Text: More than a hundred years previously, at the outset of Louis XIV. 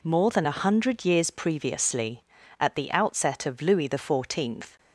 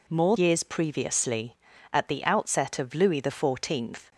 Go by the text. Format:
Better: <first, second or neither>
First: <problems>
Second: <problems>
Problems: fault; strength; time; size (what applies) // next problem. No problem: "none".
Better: first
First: none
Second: skips "than a hundred"; at 0.3 s